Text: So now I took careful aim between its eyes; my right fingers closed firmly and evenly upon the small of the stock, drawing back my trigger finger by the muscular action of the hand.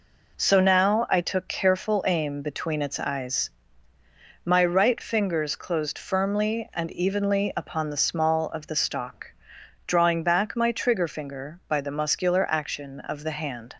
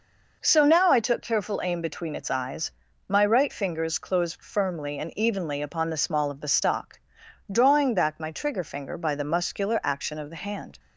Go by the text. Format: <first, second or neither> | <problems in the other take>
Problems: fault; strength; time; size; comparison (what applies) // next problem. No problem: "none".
neither | none